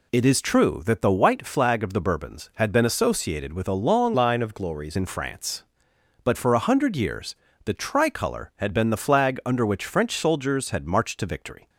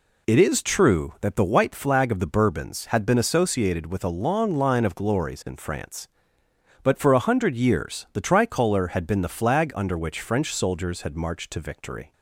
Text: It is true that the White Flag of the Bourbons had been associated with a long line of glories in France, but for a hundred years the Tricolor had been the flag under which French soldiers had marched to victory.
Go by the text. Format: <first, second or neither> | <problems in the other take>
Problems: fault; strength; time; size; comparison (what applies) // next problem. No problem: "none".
second | changes voice from "line" to "glories"; from 4.1 to 4.9 s; 0.8 s long // pauses between "years" and "the"; slight; at 7.3 s; 0.30 s long